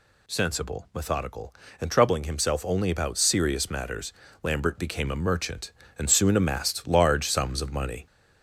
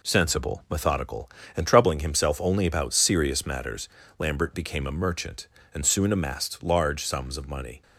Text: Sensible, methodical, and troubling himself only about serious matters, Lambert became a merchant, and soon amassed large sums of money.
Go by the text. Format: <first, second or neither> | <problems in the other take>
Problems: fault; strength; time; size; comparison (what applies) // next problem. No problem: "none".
second | gets louder; throughout; 4 dB